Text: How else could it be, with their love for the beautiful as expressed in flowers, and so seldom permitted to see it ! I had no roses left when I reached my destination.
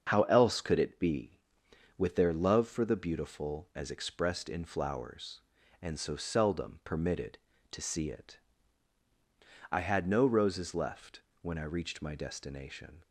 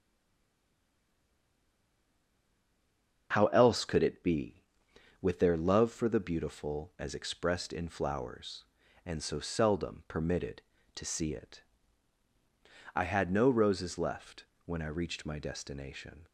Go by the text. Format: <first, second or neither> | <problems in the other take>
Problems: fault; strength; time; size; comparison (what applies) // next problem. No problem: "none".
first | stays silent before the first word; strong; until 3.3 s; 3.3 s long // starts louder than the rest; until 4.3 s; 6.5 dB; also in the first // pauses between "left" and "when"; slight; at 14.4 s; 0.22 s long; slight in the first